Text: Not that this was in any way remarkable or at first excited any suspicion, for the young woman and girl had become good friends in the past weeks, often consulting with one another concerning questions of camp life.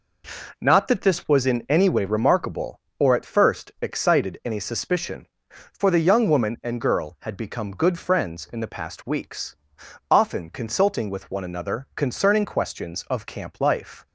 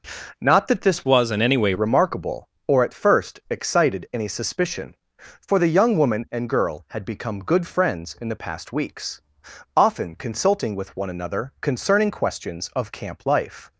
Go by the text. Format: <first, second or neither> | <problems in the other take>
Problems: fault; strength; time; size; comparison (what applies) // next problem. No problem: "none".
first | changes voice from "was" to "way"; from 1.0 to 1.7 s; 0.7 s long